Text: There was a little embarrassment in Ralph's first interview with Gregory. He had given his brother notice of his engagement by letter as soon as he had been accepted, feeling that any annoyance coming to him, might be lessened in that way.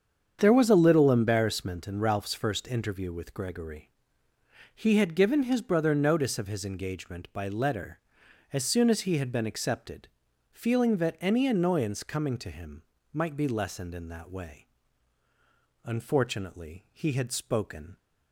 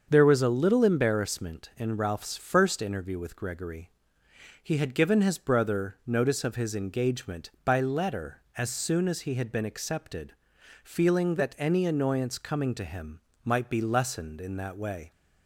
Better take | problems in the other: second | starts louder than the rest; strong; until 1.4 s; 7.5 dB; also in the second // goes on to say "Unfortunately he had spoken"; strong; from 15.8 s on; 2.1 s long

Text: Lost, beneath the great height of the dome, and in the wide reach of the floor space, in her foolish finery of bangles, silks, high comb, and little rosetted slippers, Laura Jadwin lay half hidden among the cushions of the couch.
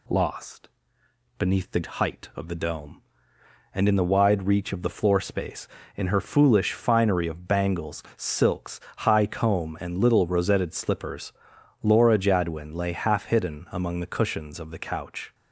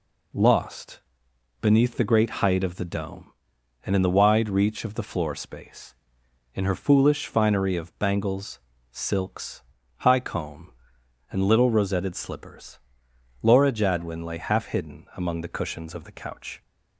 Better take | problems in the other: second | skips "great"; at 1.8 s

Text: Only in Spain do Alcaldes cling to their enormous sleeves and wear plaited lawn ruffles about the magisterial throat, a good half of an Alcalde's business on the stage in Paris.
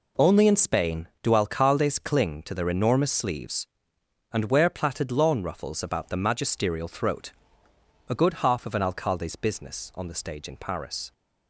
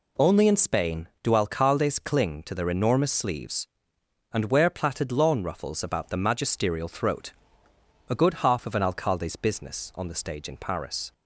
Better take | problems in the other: second | gets quieter; strong; throughout; 10 dB

